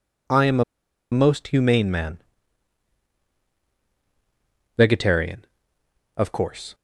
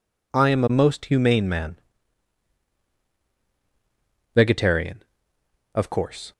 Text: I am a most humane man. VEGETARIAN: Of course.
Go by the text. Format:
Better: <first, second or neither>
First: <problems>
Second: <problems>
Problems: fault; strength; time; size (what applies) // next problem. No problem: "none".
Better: second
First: pauses between "a" and "most"; noticeable; at 0.6 s; 0.48 s long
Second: none